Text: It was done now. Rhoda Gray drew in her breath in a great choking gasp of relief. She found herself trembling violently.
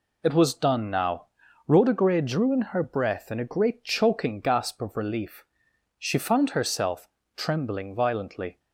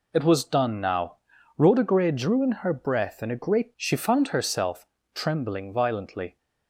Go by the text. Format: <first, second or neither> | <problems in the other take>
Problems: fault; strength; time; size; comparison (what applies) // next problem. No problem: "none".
first | skips "choking gasp of relief"; at 3.7 s // pauses between "herself" and "trembling"; slight; at 4.8 s; 0.28 s long; slight in the first